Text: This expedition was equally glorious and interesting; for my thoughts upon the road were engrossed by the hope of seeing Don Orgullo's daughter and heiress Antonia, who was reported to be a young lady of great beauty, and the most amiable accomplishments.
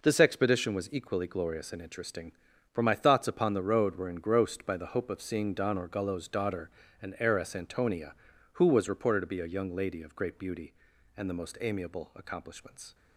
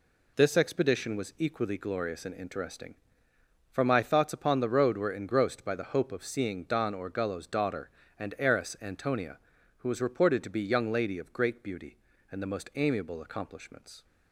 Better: first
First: none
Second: skips "a"; at 10.6 s

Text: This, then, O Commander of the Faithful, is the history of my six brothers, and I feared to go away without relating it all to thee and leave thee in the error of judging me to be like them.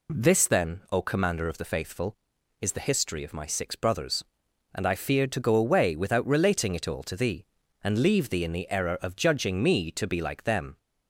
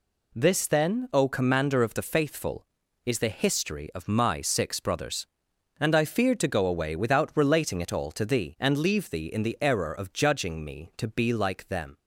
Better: neither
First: none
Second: none

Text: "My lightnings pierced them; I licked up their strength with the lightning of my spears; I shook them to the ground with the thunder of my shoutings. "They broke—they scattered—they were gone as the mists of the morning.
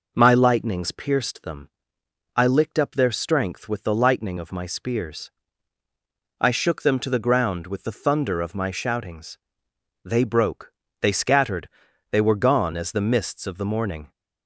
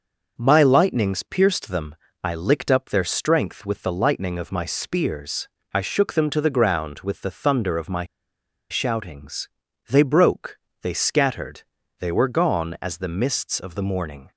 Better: first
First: none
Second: starts louder than the rest; noticeable; until 1.3 s; 6 dB // pauses between "my" and "shoutings"; noticeable; at 8.0 s; 0.65 s long

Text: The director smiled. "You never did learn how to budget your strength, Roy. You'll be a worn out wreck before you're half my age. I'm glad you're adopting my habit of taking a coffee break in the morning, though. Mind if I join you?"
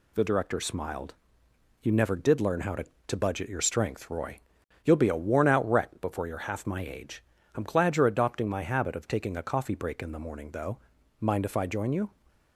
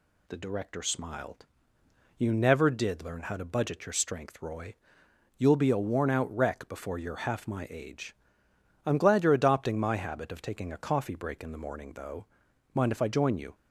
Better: second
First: says "to" twice; at 3.0 s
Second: none

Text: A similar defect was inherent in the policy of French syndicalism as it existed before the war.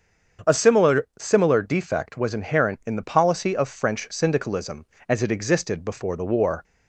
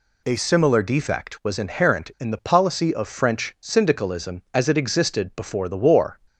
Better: second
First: starts louder than the rest; strong; until 1.6 s; 7.5 dB // says "similar" twice; at 1.1 s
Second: none

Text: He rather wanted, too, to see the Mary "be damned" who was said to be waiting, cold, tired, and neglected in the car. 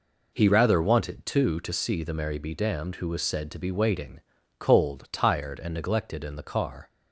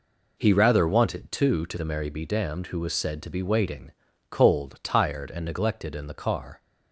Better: first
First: none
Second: skips "see"; at 1.7 s

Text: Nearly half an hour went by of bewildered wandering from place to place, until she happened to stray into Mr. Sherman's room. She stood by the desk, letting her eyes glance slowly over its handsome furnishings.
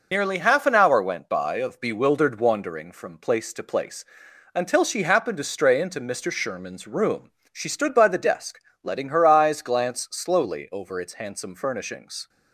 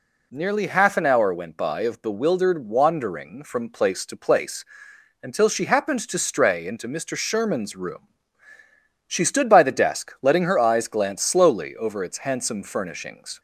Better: second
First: loses the start of "Nearly"; at 0.1 s; 90 ms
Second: none

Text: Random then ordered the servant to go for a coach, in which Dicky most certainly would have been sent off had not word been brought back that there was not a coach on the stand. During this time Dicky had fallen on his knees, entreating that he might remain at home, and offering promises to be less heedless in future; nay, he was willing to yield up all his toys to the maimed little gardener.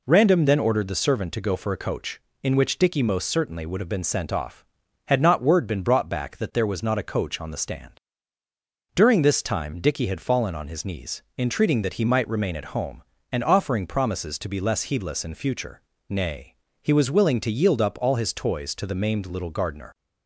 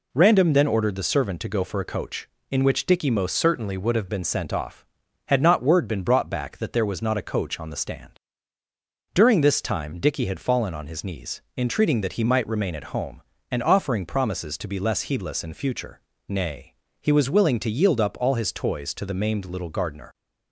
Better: first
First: none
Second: changes voice from "certainly" to "have"; from 3.3 to 4.0 s; 0.7 s long

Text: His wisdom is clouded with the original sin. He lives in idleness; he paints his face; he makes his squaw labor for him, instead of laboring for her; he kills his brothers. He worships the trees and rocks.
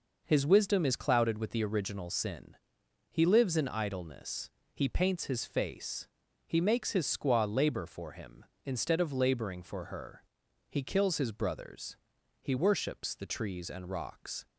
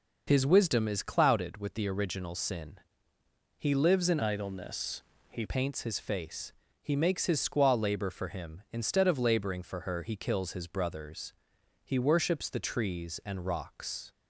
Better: first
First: none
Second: changes voice from "idleness" to "he"; from 4.2 to 5.4 s; 1.2 s long

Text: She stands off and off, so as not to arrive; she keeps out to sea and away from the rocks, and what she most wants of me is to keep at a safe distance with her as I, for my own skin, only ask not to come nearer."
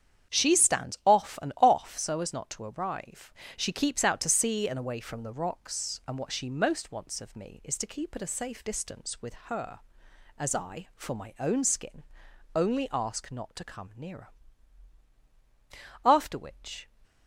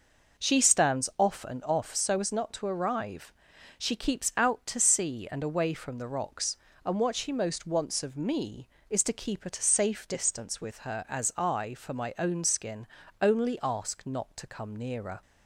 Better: second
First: starts louder than the rest; strong; until 1.3 s; 8.5 dB // goes on to say "After which"; noticeable; from 16.0 s on; 0.86 s long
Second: none

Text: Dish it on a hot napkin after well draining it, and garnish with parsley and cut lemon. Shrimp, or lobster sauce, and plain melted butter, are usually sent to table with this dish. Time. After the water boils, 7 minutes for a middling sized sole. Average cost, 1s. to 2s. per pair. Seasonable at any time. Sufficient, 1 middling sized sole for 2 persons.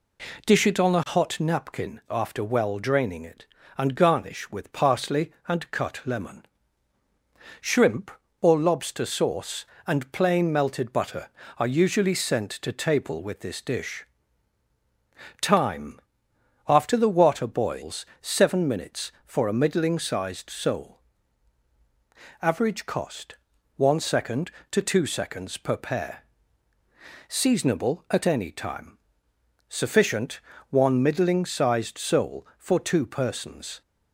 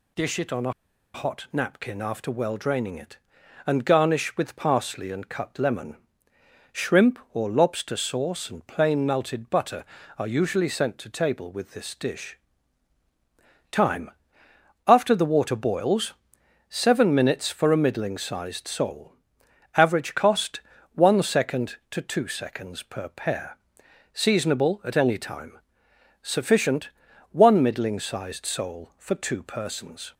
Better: first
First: none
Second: pauses between "a" and "hot"; at 0.7 s; 0.42 s long

